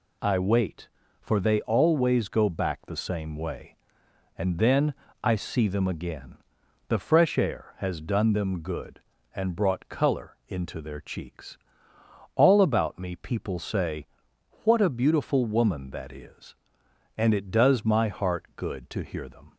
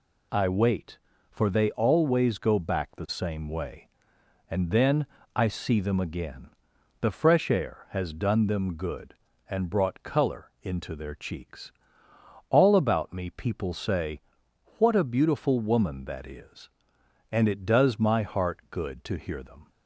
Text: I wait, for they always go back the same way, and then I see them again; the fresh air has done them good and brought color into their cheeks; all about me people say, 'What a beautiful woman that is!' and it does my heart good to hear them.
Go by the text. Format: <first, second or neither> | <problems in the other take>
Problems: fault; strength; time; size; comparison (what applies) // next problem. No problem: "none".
neither | pauses between "then" and "I"; slight; the same in both